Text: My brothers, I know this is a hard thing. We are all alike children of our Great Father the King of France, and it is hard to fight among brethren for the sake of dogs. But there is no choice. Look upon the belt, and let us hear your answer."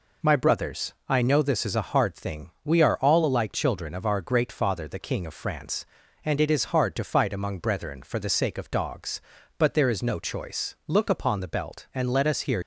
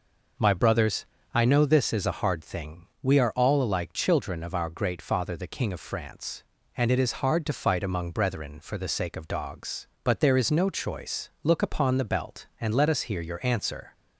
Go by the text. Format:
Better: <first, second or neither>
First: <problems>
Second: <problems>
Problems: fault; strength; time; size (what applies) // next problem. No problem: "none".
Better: second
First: stops before "your answer"; at 12.6 s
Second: none